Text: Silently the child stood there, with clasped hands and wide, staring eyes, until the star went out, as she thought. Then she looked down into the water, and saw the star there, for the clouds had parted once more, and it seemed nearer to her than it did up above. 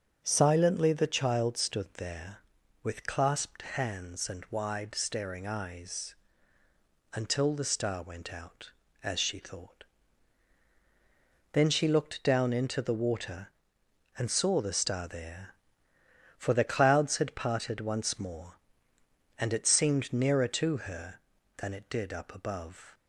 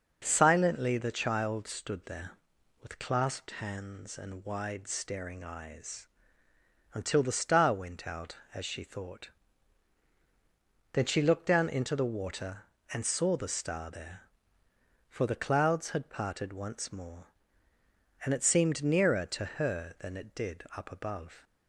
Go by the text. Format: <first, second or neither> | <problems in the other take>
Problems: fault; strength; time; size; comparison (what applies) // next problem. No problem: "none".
neither | starts louder than the rest; the same in both